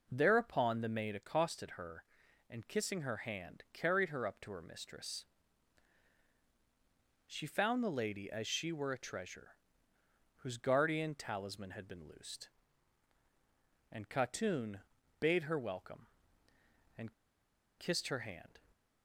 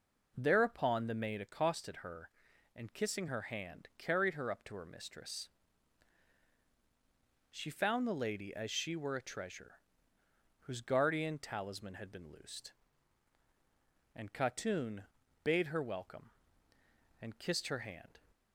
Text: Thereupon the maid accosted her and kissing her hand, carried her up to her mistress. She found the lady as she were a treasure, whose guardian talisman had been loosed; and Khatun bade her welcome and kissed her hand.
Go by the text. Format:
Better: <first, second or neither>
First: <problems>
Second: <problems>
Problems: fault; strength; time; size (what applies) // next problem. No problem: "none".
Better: second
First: pauses between "Khatun" and "bade"; at 14.8 s; 0.40 s long // pauses between "and" and "kissed"; noticeable; at 17.1 s; 0.64 s long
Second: pauses between "Khatun" and "bade"; at 15.0 s; 0.40 s long